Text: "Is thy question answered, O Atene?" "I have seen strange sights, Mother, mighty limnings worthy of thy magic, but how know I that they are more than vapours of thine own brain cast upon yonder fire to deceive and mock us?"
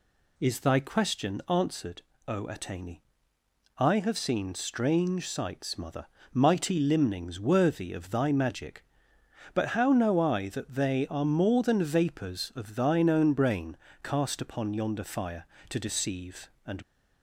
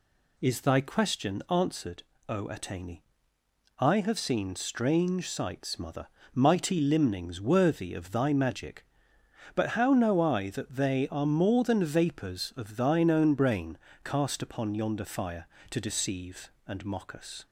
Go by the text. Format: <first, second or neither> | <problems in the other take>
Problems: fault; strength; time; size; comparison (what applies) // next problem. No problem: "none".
second | pauses between "brain" and "cast"; slight; at 13.7 s; 0.26 s long; slight in the second // stops before "mock us"; at 16.8 s